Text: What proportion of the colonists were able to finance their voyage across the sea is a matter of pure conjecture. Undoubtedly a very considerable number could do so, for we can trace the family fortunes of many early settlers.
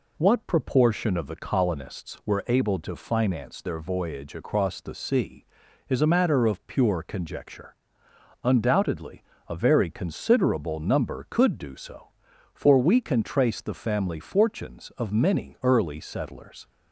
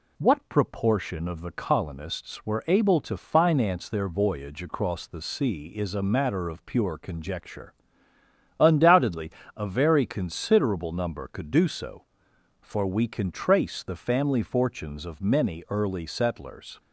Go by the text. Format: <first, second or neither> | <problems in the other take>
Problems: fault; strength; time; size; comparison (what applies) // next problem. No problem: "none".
neither | pauses between "Undoubtedly" and "a"; slight; the same in both